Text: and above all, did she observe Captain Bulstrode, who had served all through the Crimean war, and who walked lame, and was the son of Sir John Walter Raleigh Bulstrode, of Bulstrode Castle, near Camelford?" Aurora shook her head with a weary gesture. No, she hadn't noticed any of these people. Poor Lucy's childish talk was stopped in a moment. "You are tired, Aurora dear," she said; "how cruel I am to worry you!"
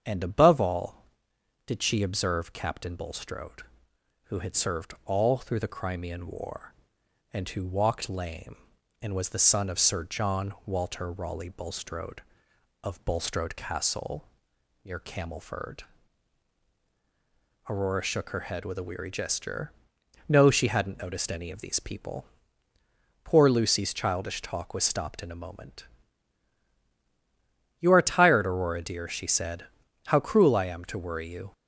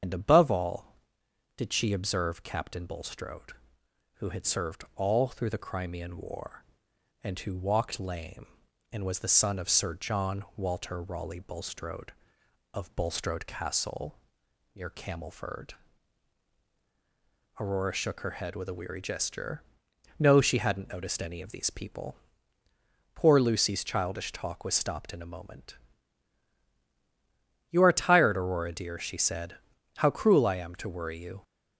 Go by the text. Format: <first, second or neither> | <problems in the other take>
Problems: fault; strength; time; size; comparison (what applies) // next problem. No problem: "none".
first | loses the start of "and"; at 0.0 s; 70 ms // starts louder than the rest; strong; until 1.6 s; 7.5 dB; strong in the first